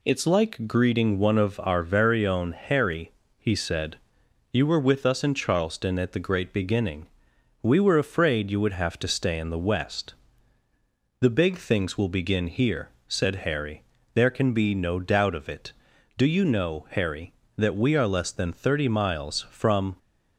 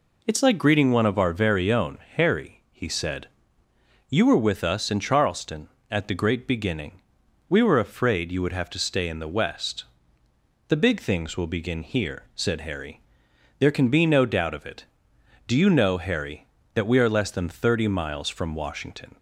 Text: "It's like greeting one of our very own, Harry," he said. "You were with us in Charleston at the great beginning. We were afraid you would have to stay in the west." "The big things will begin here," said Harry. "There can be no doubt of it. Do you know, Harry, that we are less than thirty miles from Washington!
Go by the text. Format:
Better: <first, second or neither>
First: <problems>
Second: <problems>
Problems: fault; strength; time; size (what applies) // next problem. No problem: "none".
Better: second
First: stops before "Washington"; at 19.9 s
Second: none